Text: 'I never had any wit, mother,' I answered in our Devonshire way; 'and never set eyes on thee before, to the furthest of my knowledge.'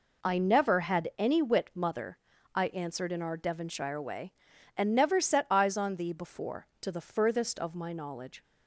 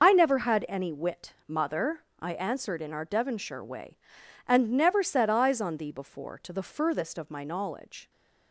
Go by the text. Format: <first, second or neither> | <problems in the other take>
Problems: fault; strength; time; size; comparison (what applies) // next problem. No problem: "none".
first | loses the start of "I"; at 0.0 s; 35 ms